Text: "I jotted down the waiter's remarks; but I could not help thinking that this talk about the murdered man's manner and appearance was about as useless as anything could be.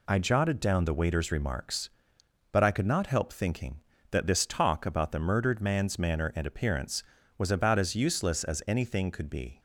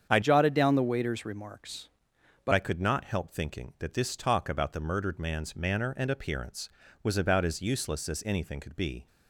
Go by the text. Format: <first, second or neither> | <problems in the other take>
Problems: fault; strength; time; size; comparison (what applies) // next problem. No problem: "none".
first | starts louder than the rest; strong; until 1.1 s; 7.5 dB // changes voice from "jotted" to "but"; from 0.2 to 2.5 s; 2.3 s long